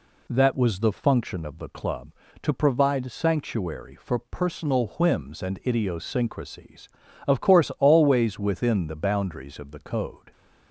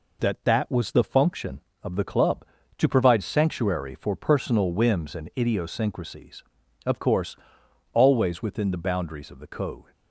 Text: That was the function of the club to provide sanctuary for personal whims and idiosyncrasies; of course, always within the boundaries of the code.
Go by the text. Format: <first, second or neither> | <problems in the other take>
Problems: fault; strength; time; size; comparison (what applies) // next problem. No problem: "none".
first | says "That" twice; at 0.4 s